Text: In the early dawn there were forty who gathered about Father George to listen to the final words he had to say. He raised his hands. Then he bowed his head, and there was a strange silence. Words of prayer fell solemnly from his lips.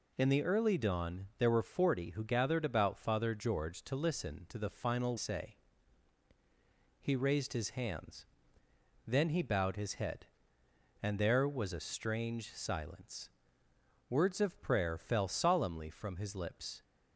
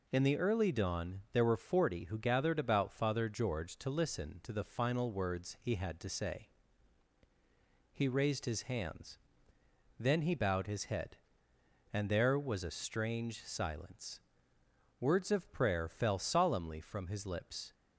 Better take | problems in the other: second | skips "words he had to"; at 5.1 s

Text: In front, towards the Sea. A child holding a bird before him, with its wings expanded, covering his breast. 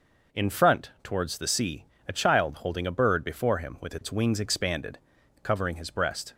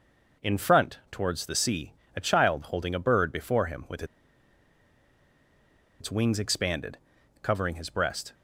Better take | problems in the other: first | pauses between "with" and "its"; strong; at 4.0 s; 1.9 s long

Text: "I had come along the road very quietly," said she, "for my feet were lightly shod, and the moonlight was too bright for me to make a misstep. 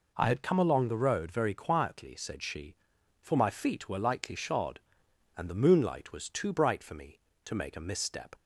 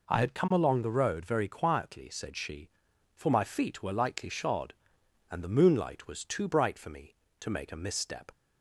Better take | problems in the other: neither | none

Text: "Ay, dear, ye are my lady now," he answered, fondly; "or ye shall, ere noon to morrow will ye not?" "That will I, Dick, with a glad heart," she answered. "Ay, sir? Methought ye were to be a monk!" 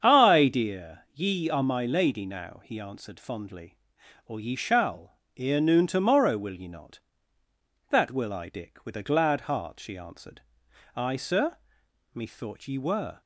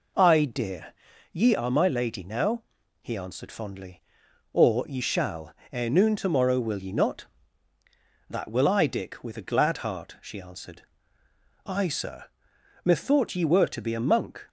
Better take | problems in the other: second | starts louder than the rest; strong; until 1.0 s; 7.5 dB // stops before "to be a monk"; at 13.2 s

